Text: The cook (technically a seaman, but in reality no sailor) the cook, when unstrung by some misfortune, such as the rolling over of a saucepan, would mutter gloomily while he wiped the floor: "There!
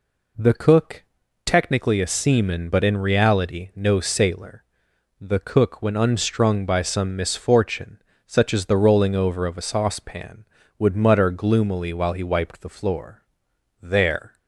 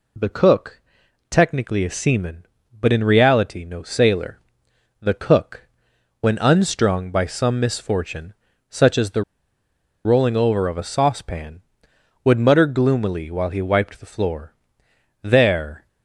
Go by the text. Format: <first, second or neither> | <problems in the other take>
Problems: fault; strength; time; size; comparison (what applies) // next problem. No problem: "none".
first | pauses between "the" and "rolling"; noticeable; at 9.2 s; 0.84 s long